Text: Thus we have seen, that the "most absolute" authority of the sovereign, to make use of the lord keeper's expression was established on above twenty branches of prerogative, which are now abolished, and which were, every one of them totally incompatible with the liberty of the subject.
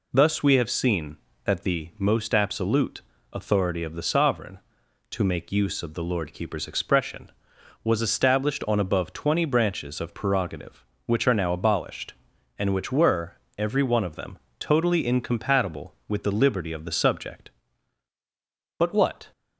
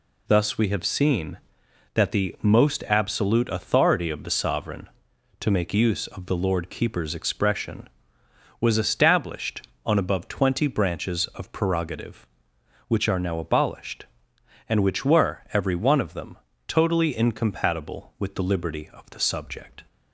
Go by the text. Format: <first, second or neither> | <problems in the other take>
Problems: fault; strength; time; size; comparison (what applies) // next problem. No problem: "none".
second | pauses between "absolute" and "authority"; slight; at 2.9 s; 0.32 s long // pauses between "them" and "totally"; slight; at 14.3 s; 0.22 s long; slight in the second // goes on to say "But what"; from 18.7 s on; 0.54 s long